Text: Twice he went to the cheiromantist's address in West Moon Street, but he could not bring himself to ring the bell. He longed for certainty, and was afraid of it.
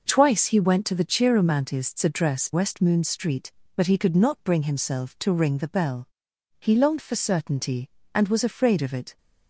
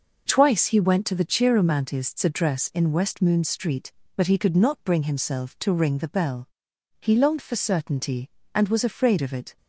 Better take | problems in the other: second | skips "in"; at 2.5 s

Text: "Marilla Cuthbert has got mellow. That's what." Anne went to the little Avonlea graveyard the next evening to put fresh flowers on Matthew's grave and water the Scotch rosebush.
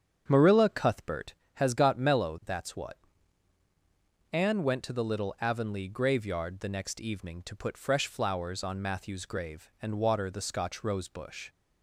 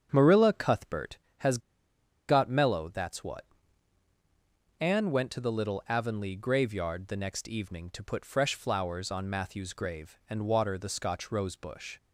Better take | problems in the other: first | starts louder than the rest; strong; until 1.1 s; 8.5 dB; strong in the first // pauses between "has" and "got"; noticeable; at 1.5 s; 0.69 s long

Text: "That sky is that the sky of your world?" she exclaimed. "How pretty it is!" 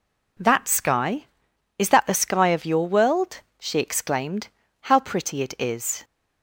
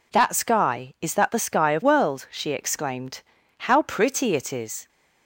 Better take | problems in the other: first | skips "your"; at 1.8 s

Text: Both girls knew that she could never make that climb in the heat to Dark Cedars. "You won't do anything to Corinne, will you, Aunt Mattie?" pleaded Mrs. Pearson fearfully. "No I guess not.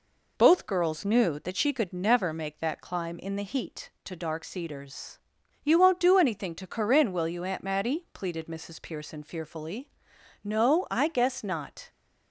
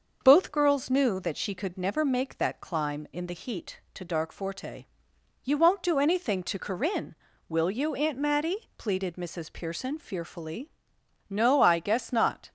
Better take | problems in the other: first | starts louder than the rest; noticeable; until 1.2 s; 6 dB // says "Forte" for "Cedars"; at 4.3 s

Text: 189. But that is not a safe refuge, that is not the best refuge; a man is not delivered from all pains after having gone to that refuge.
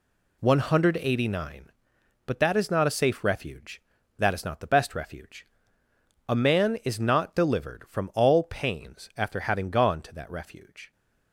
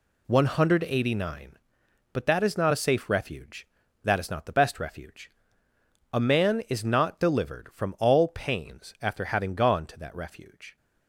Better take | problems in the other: neither | none

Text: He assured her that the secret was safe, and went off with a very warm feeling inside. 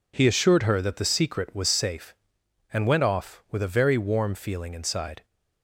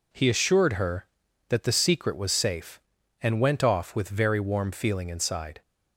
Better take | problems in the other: first | skips "a"; at 4.0 s

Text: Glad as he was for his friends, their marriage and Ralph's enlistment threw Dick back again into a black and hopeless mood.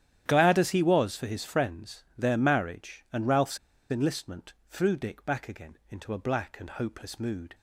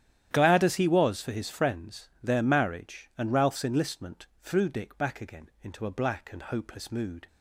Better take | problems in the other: second | starts louder than the rest; strong; until 1.2 s; 11 dB; strong in the second // pauses between "Ralph's" and "enlistment"; slight; at 3.5 s; 0.34 s long // pauses between "enlistment" and "threw"; slight; at 4.5 s; 0.16 s long; slight in the second

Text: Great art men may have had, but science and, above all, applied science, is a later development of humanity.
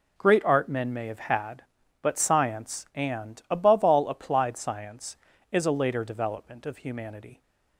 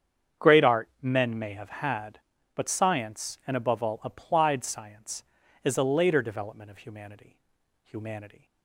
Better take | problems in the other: first | starts louder than the rest; strong; until 1.5 s; 8 dB // says "humanity" twice; at 7.8 s

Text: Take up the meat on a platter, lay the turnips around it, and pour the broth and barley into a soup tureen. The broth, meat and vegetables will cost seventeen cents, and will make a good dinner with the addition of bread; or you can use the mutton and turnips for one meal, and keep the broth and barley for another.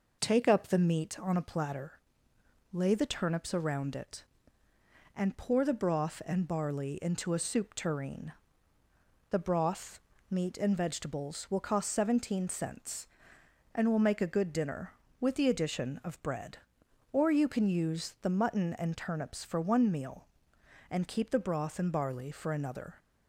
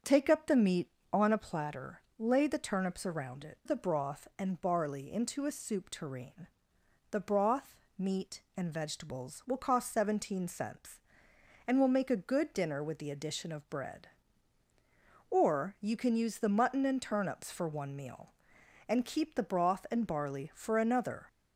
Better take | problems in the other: first | starts louder than the rest; strong; until 1.2 s; 7 dB // skips "and pour"; at 3.6 s

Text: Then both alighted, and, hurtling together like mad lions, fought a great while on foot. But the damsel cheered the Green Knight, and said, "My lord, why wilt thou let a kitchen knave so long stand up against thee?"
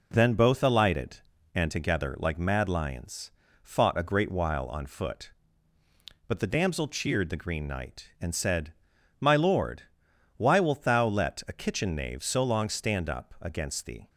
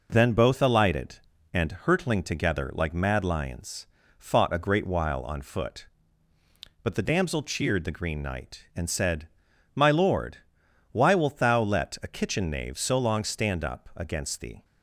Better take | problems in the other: second | skips "hurtling"; at 1.7 s

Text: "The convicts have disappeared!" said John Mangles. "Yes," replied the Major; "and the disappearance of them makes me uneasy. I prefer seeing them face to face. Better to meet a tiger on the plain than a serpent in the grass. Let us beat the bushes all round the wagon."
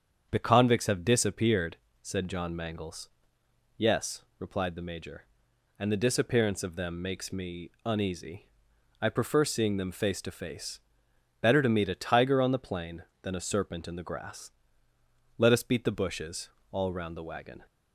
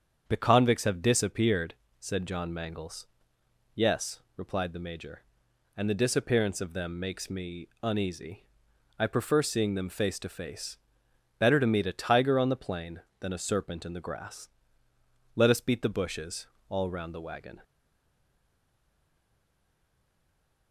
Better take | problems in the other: first | starts louder than the rest; strong; until 1.2 s; 7.5 dB; strong in the first // pauses between "me" and "uneasy"; slight; at 7.6 s; 0.16 s long; slight in the first // pauses between "bushes" and "all"; slight; at 16.4 s; 0.22 s long; slight in the first // stays silent after the last word; strong; from 17.6 s on; 3.1 s long

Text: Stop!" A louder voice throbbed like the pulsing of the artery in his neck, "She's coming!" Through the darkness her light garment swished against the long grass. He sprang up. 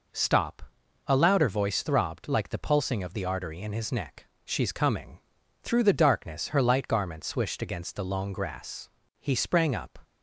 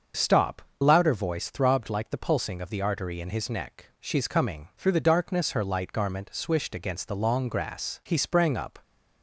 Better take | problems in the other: first | starts louder than the rest; until 1.3 s; 6.5 dB // skips "A"; at 0.7 s

